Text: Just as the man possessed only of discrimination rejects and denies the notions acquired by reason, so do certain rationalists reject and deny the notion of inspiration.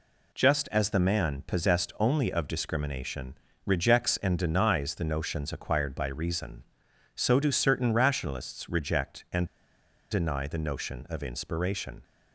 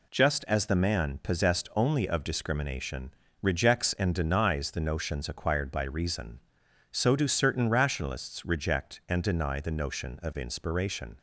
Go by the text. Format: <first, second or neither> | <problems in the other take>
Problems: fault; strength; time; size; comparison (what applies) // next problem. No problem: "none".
second | pauses between "discrimination" and "rejects"; slight; at 3.3 s; 0.30 s long; slight in the second // pauses between "and" and "deny"; noticeable; at 9.4 s; 0.65 s long